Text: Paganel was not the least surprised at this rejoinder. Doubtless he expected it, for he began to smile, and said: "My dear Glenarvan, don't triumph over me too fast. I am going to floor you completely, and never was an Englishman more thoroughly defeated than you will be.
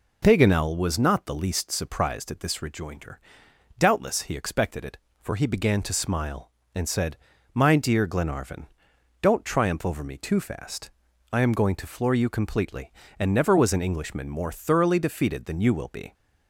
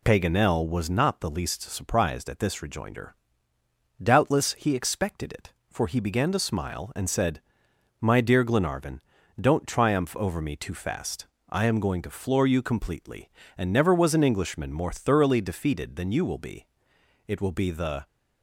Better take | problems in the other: first | goes on to say "It will be the"; noticeable; from 17.2 s on; 0.80 s long

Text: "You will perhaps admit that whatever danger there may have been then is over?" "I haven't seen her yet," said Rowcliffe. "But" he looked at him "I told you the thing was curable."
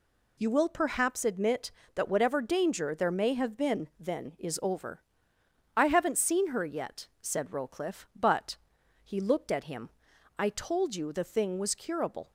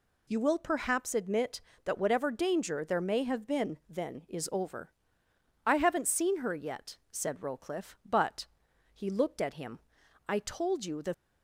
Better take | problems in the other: first | pauses between "But" and "he"; noticeable; at 8.4 s; 0.46 s long; noticeable in the first // pauses between "him" and "I"; noticeable; at 9.8 s; 0.48 s long; noticeable in the first // stops before "thing was curable"; at 11.1 s

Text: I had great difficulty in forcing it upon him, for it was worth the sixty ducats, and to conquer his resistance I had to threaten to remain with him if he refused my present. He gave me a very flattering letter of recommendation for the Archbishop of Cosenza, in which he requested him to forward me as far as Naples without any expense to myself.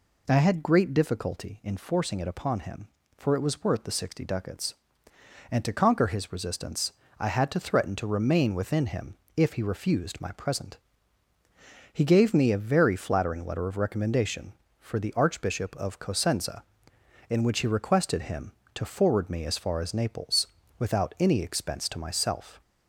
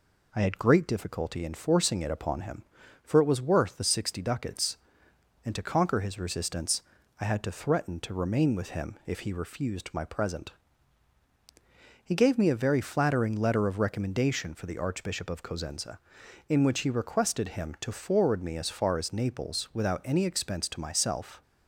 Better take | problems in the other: second | pauses between "resistance" and "I"; slight; at 6.9 s; 0.28 s long; also in the second // says "within" for "with"; at 8.5 s // pauses between "him" and "if"; slight; at 9.1 s; 0.22 s long // pauses between "Naples" and "without"; slight; at 20.4 s; 0.30 s long

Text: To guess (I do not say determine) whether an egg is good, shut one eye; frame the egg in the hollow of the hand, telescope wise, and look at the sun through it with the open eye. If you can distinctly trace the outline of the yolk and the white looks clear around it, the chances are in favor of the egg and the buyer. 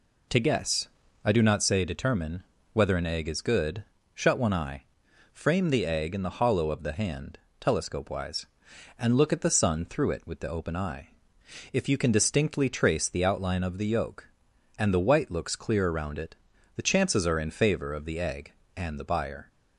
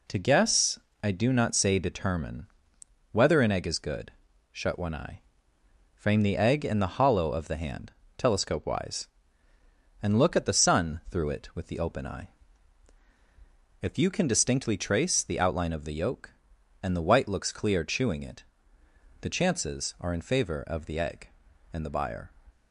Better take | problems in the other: first | says "chewing" for "around"; at 17.8 s

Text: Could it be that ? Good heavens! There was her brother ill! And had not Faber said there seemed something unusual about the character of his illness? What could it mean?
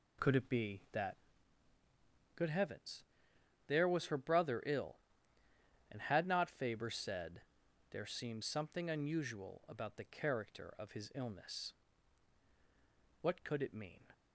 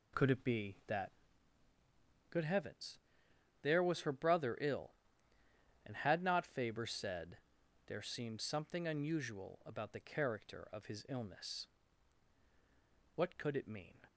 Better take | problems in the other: neither | pauses between "said" and "there"; noticeable; the same in both

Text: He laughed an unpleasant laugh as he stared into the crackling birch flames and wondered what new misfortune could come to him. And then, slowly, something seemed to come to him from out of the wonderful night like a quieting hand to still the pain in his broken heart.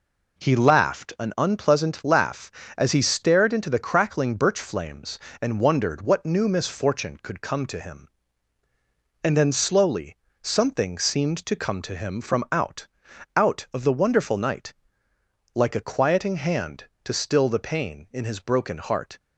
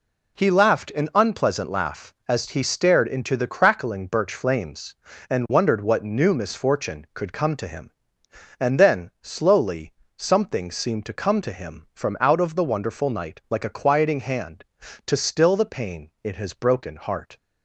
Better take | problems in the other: second | says "out" twice; at 13.3 s // pauses between "night" and "like"; noticeable; at 14.7 s; 0.80 s long

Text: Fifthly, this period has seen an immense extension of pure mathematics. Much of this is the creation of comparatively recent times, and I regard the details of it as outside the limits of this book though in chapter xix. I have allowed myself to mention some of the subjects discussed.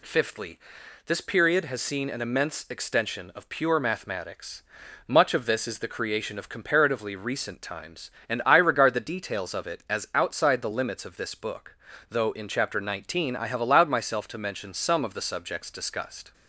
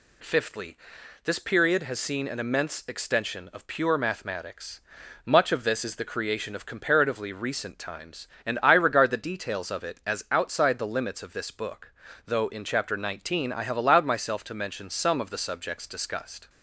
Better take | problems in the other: neither | pauses between "book" and "though"; slight; the same in both

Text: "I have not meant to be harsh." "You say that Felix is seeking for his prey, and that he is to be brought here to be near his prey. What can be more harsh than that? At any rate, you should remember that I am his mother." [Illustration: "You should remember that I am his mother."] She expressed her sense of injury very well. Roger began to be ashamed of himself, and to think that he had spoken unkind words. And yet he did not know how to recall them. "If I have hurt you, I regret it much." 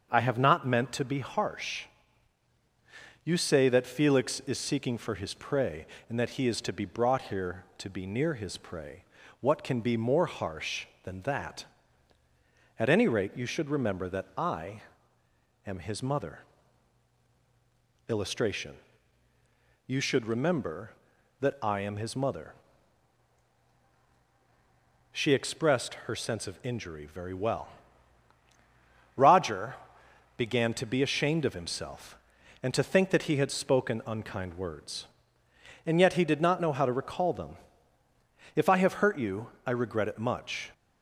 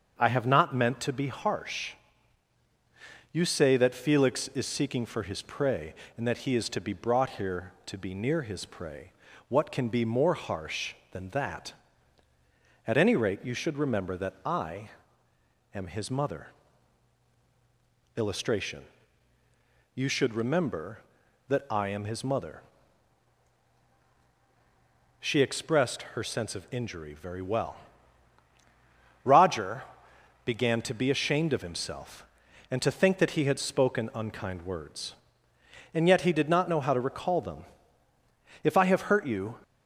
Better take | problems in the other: first | starts louder than the rest; until 1.1 s; 7 dB; also in the first // pauses between "I" and "am"; noticeable; at 14.9 s; 0.84 s long; noticeable in the first // pauses between "Roger" and "began"; noticeable; at 29.8 s; 0.62 s long; noticeable in the first // stops before "I regret it much"; at 39.6 s

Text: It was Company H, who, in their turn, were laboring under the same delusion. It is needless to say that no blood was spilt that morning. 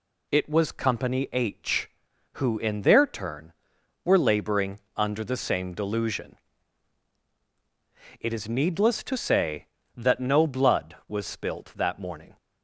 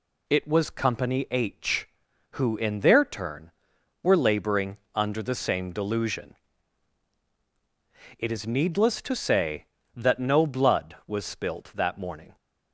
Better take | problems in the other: neither | pauses between "laboring" and "under"; slight; the same in both

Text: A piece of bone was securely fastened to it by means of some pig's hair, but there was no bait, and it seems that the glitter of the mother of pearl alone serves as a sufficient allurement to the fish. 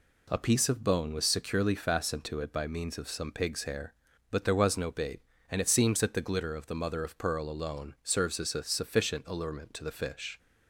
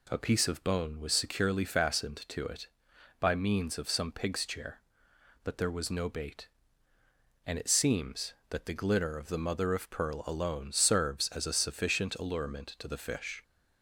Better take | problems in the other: first | says "chair" for "hair"; at 4.4 s

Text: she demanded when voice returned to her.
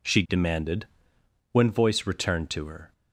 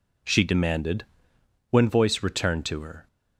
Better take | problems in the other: neither | pauses between "demanded" and "when"; noticeable; the same in both

